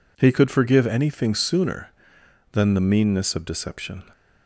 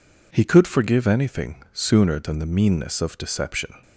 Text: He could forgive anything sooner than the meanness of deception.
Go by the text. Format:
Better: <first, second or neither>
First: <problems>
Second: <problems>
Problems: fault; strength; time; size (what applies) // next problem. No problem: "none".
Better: neither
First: none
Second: none